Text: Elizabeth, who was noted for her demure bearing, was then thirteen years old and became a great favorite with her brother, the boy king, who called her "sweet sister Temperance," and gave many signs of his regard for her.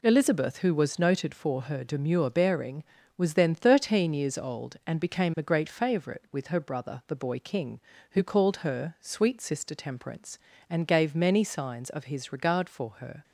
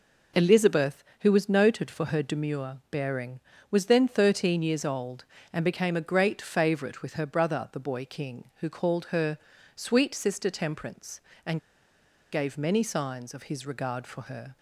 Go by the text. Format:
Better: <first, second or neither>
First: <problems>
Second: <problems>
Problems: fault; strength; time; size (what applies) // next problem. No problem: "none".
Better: first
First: none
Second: pauses between "her" and "sweet"; at 9.3 s; 0.38 s long // pauses between "and" and "gave"; noticeable; at 11.5 s; 0.73 s long